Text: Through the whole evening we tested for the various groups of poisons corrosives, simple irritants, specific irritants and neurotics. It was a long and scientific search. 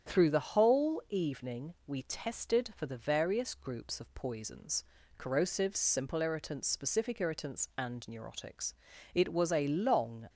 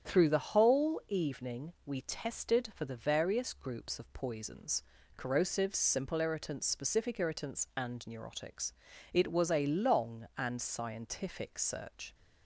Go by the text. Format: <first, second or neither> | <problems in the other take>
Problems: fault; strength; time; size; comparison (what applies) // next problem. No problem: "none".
second | starts louder than the rest; strong; until 1.1 s; 8.5 dB; strong in the second // pauses between "poisons" and "corrosives"; slight; at 4.8 s; 0.34 s long; slight in the second // stops before "and scientific search"; at 10.2 s